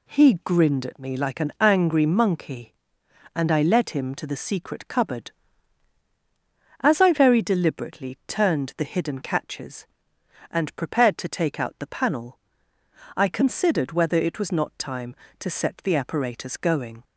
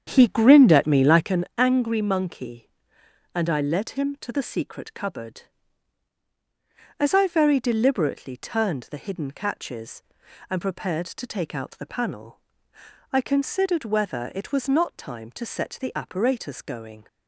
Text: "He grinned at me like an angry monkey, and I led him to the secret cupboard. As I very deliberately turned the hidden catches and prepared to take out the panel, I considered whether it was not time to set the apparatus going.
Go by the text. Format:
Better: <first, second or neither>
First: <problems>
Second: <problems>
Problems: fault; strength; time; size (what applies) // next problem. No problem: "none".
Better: first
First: none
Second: starts louder than the rest; strong; until 1.5 s; 8 dB